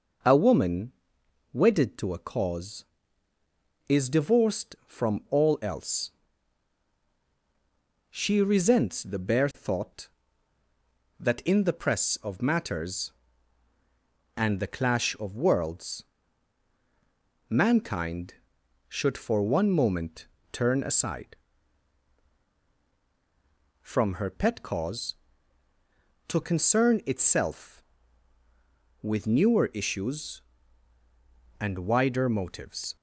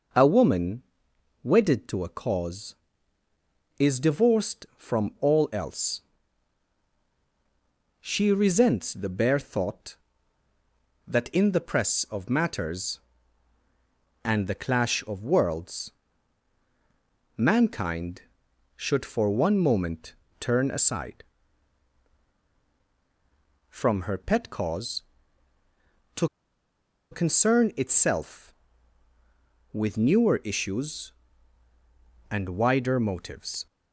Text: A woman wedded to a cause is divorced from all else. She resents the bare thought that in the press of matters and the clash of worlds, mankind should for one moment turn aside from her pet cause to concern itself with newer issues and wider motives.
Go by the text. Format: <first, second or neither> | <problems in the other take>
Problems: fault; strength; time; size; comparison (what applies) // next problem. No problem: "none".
first | pauses between "woman" and "wedded"; noticeable; at 0.8 s; 0.58 s long; noticeable in the first // pauses between "moment" and "turn"; slight; at 20.1 s; 0.26 s long; slight in the first // pauses between "to" and "concern"; noticeable; at 26.2 s; 0.84 s long